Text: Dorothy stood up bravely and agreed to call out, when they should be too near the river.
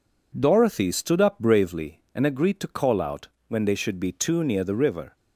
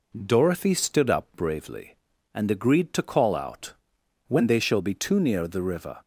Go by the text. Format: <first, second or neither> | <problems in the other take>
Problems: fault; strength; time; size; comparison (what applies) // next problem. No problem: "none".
first | says "shall" for "should"; at 4.5 s